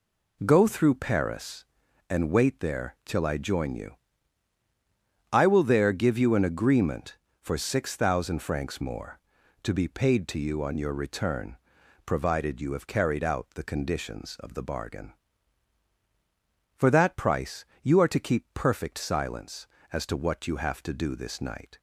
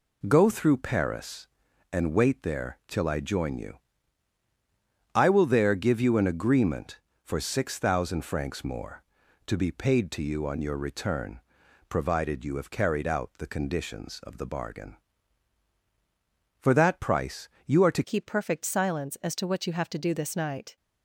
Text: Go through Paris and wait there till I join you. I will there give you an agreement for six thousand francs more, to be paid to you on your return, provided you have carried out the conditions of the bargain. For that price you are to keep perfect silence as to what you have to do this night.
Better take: first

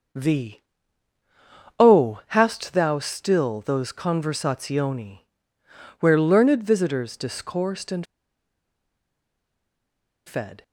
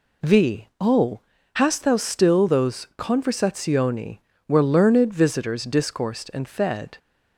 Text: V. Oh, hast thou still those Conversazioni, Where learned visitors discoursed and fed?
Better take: second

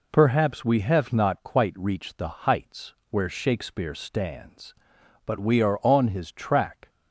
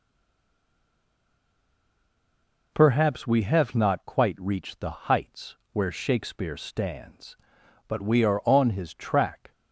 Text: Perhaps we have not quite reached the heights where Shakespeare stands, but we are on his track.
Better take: first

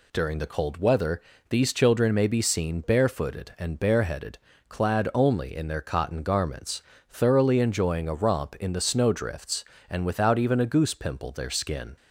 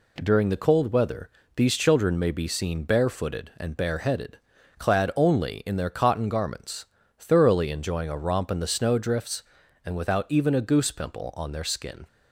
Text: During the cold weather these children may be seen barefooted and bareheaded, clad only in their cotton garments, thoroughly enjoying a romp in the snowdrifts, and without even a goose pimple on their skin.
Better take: second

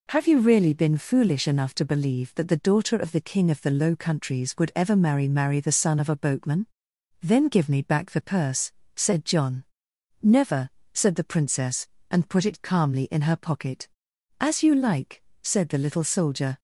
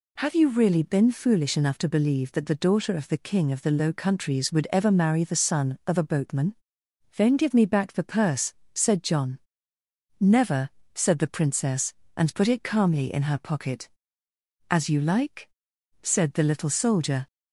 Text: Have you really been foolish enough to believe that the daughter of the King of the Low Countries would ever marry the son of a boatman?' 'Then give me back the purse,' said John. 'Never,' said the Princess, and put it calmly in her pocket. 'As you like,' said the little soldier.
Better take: second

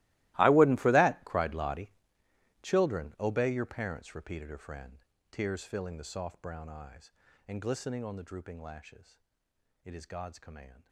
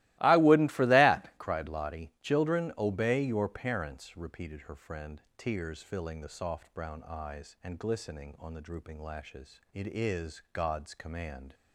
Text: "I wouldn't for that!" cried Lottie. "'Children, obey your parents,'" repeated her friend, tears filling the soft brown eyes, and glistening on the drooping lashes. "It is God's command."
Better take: second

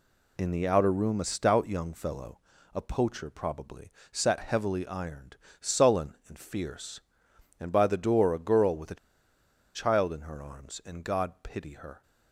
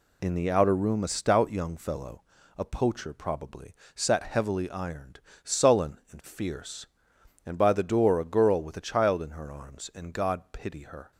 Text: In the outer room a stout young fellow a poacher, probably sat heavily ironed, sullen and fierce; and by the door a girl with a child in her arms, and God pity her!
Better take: second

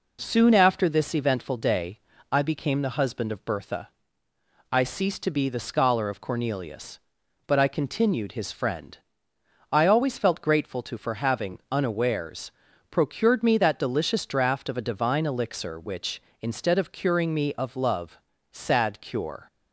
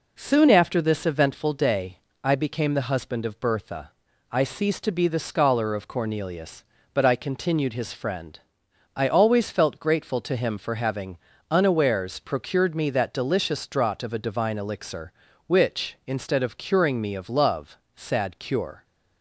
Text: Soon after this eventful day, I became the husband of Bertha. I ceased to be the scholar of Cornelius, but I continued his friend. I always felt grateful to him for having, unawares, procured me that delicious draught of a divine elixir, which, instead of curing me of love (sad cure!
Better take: second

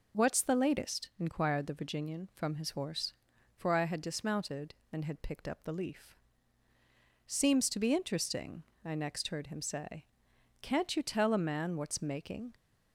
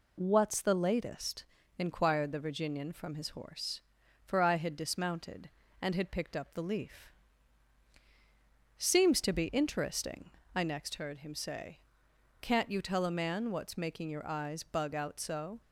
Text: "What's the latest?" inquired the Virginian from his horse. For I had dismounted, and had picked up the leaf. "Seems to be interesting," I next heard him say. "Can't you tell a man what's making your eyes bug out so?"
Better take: second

